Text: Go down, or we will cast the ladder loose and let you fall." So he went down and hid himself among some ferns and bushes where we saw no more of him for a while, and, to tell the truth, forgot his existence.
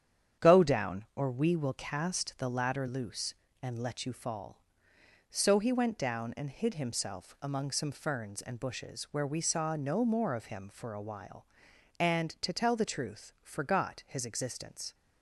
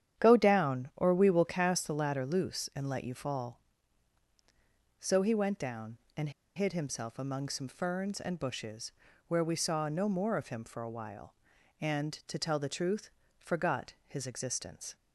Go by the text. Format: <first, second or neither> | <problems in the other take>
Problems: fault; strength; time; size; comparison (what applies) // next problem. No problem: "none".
first | starts louder than the rest; strong; until 1.2 s; 9.5 dB; strong in the first // pauses between "and" and "hid"; slight; at 6.2 s; 0.26 s long // pauses between "bushes" and "where"; slight; at 8.9 s; 0.34 s long